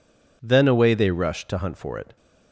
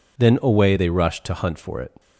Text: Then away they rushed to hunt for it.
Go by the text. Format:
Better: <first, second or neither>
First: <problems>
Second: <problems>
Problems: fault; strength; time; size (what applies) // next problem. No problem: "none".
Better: neither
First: none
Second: none